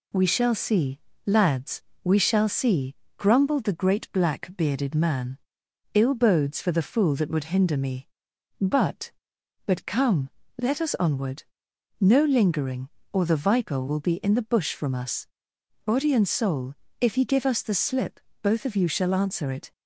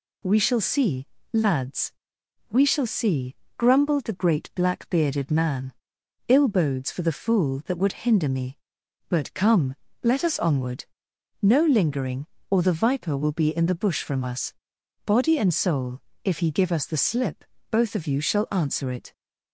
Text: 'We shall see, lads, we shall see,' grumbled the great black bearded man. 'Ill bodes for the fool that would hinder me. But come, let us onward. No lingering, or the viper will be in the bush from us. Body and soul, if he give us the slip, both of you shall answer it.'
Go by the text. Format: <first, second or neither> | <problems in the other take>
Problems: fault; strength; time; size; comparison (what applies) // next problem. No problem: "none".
second | says "But" twice; at 9.6 s